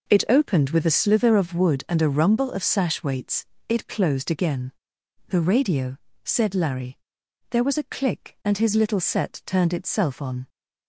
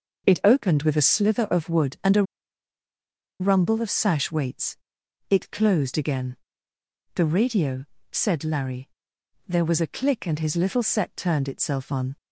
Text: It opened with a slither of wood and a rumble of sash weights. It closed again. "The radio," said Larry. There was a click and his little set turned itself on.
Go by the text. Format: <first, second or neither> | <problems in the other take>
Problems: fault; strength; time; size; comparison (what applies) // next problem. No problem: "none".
first | pauses between "a" and "rumble"; at 2.2 s; 1.1 s long